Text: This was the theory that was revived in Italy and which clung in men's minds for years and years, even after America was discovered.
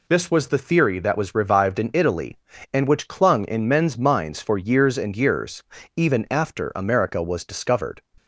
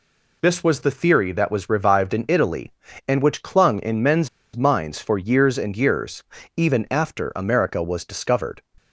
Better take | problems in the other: first | pauses between "men's" and "minds"; slight; at 4.2 s; 0.27 s long

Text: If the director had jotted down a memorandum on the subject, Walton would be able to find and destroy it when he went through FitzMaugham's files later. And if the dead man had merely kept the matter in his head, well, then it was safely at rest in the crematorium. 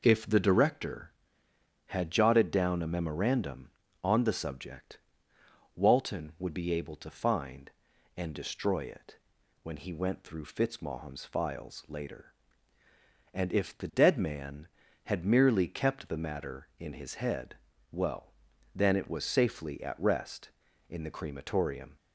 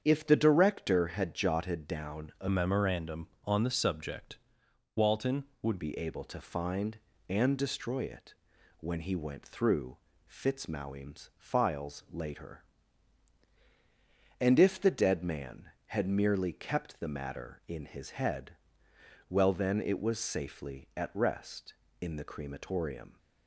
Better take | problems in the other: first | starts louder than the rest; strong; until 1.0 s; 7.5 dB // changes voice from "memorandum" to "would"; from 2.4 to 5.7 s; 3.3 s long // pauses between "it" and "when"; noticeable; at 8.3 s; 0.46 s long; noticeable in the first // pauses between "through" and "FitzMaugham's"; slight; at 9.9 s; 0.34 s long

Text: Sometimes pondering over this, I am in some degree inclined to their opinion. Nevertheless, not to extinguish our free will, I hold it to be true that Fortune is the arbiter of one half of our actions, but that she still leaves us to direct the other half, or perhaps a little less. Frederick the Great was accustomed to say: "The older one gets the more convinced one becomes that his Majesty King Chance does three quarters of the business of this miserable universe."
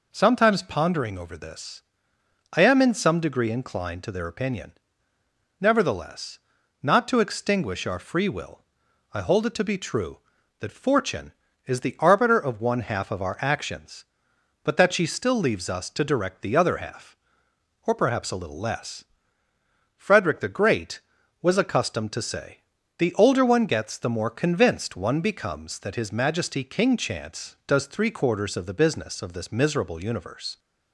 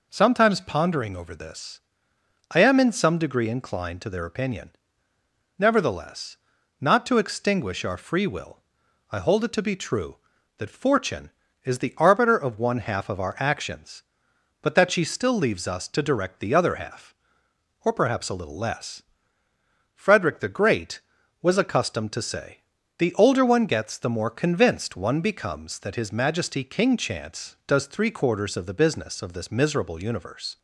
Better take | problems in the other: neither | none

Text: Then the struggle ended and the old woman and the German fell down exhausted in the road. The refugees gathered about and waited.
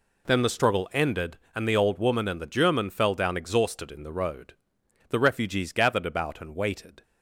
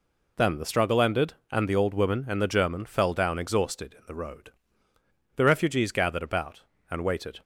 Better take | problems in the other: neither | none

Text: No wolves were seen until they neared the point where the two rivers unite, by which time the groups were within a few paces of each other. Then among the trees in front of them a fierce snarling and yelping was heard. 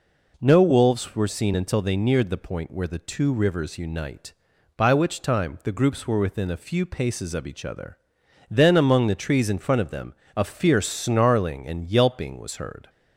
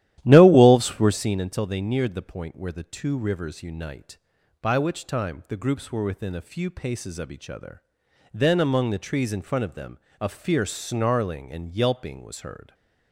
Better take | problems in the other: first | starts louder than the rest; strong; until 1.4 s; 12.5 dB // pauses between "them" and "a"; slight; at 9.9 s; 0.20 s long; slight in the first

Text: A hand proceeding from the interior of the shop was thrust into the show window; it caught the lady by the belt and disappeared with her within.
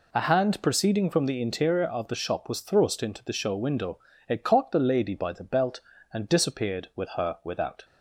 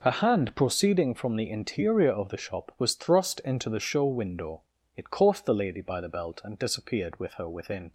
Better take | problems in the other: second | says "without" for "within"; at 7.4 s

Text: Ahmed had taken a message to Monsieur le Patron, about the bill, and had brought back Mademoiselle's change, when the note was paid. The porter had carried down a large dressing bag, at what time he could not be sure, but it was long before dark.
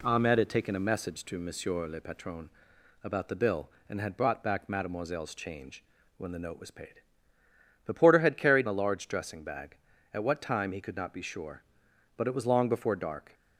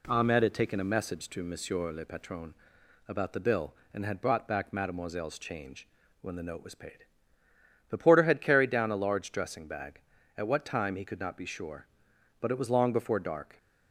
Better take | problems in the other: second | skips "down"; at 8.6 s

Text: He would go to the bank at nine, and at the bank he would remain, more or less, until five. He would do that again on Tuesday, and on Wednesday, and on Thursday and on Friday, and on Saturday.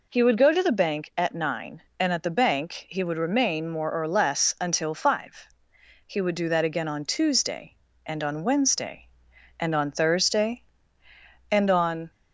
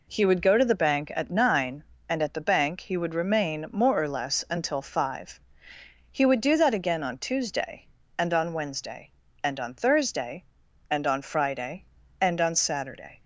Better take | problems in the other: second | stops before "Friday and on Saturday"; at 12.1 s

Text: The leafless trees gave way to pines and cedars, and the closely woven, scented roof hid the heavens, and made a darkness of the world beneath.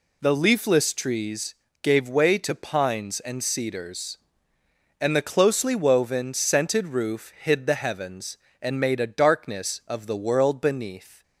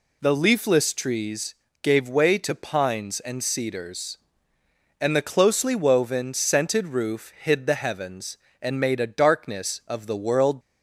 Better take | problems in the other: first | pauses between "trees" and "gave"; slight; at 1.5 s; 0.28 s long; slight in the first // stops before "beneath"; at 10.5 s

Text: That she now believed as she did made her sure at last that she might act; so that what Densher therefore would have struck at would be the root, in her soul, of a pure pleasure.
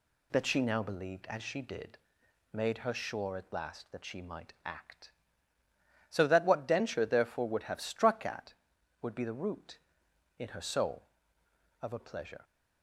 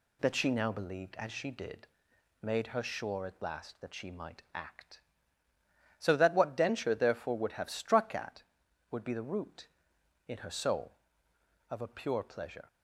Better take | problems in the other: second | pauses between "did" and "made"; noticeable; at 1.9 s; 0.56 s long; noticeable in the second // skips "pure"; at 11.9 s

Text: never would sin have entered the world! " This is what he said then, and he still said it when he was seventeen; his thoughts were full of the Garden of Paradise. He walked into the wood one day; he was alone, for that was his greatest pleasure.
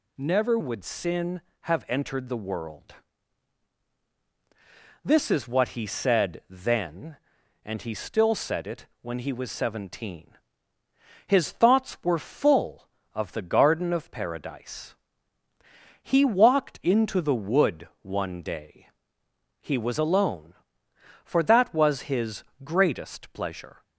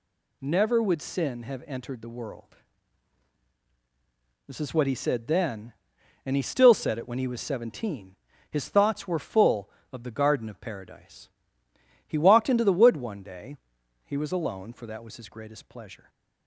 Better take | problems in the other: second | changes voice at "would"; from 0.5 s on; 23.3 s long // pauses between "it" and "when"; slight; at 8.8 s; 0.16 s long // pauses between "his" and "greatest"; slight; at 22.4 s; 0.22 s long

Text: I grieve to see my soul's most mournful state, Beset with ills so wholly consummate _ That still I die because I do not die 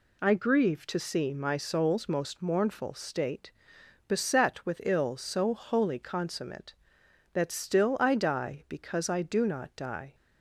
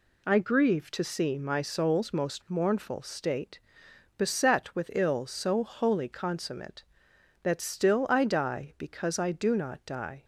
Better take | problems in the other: neither | none

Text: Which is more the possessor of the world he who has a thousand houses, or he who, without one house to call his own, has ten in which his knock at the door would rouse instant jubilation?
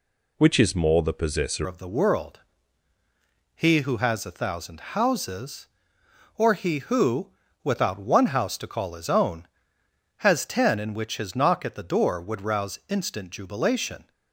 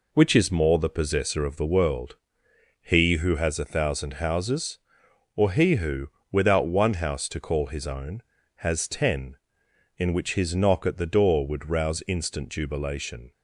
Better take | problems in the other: second | changes voice at "of"; from 1.6 s on; 12.5 s long // pauses between "world" and "he"; at 2.4 s; 1.1 s long; noticeable in the second

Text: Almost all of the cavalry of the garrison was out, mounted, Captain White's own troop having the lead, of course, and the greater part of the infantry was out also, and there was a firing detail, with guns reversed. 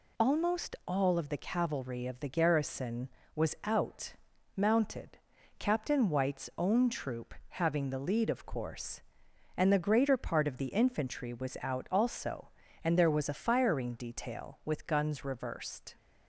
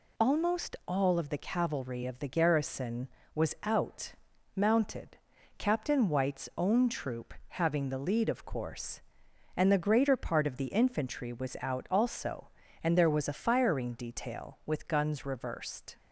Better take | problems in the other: neither | pauses between "troop" and "having"; slight; the same in both

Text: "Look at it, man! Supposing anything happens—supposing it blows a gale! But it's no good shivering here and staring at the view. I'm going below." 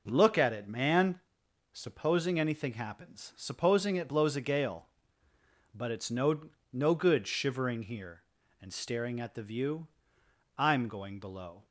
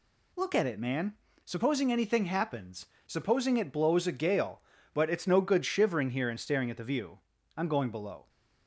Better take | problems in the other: second | says "no" twice; at 6.7 s

